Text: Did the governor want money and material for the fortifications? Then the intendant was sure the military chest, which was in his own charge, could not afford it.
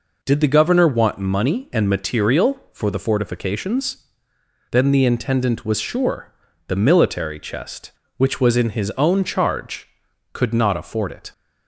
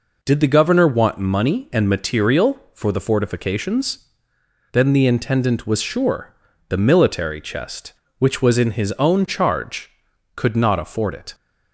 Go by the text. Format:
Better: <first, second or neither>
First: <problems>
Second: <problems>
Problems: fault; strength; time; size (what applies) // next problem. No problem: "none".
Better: neither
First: pauses between "sure" and "the"; at 6.3 s; 0.38 s long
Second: pauses between "sure" and "the"; at 6.3 s; 0.38 s long